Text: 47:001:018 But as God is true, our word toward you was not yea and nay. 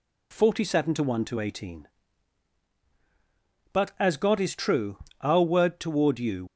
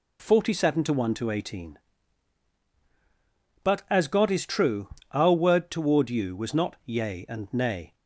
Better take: second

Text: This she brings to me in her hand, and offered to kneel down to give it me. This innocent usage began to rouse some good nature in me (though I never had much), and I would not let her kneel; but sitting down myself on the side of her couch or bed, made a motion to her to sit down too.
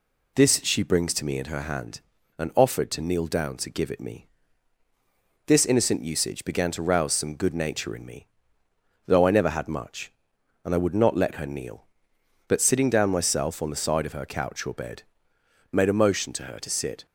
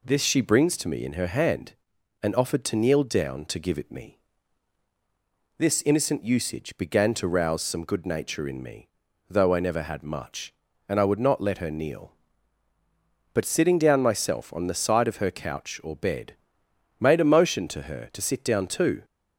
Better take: second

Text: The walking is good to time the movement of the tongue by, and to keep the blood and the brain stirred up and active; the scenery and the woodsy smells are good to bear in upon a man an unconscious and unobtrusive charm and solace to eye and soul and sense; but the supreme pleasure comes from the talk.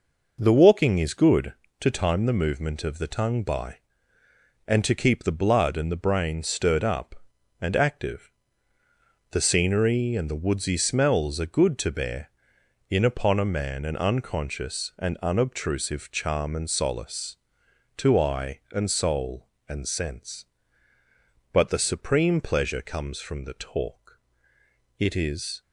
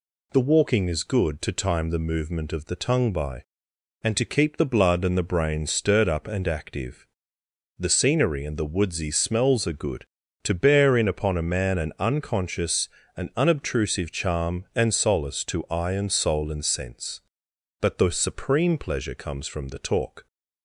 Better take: second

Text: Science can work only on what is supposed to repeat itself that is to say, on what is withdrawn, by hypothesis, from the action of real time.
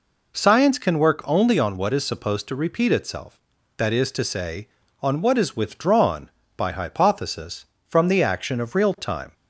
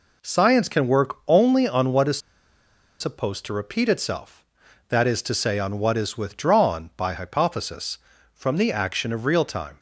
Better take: first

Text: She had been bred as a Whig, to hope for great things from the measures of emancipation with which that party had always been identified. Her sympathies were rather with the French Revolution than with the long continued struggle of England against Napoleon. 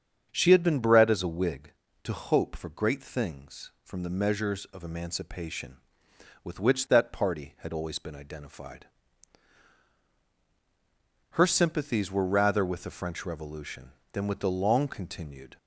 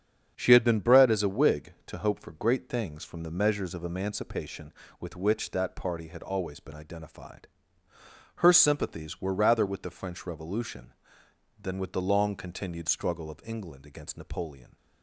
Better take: second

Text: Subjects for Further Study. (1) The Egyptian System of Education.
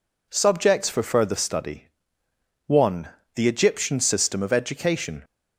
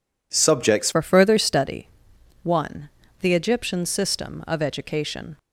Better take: first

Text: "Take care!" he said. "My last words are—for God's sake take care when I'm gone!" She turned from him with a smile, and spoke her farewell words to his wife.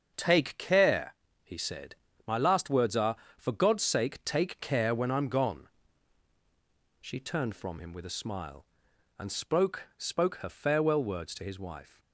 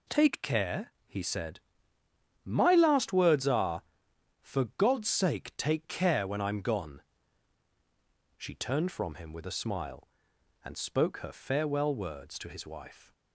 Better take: second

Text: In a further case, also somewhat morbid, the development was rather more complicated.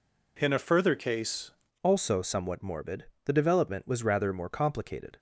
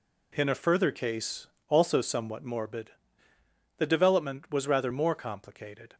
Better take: second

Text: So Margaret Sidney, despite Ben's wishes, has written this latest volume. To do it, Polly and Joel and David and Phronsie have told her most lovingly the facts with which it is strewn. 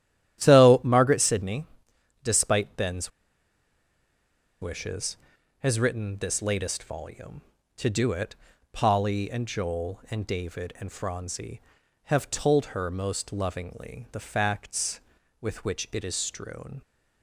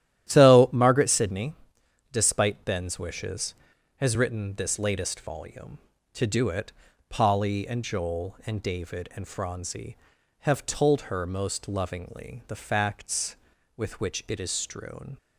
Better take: second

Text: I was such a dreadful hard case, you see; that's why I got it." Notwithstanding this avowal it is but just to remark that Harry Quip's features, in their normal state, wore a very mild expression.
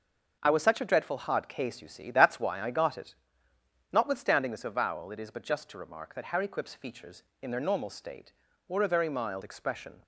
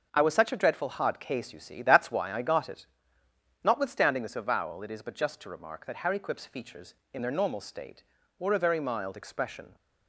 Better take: neither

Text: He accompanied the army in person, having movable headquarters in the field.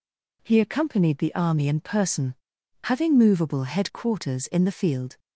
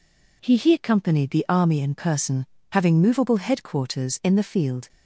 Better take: first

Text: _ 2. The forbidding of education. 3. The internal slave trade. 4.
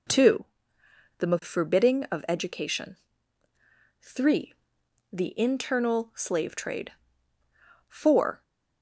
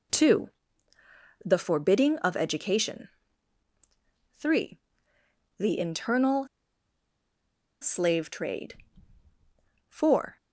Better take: first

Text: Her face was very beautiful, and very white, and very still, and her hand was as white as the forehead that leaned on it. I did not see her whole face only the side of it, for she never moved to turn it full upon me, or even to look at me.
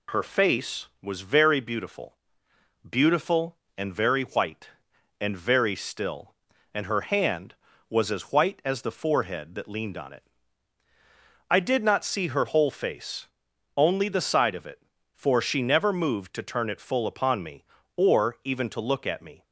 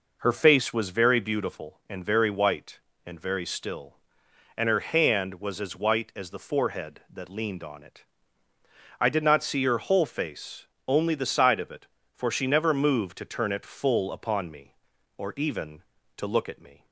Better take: second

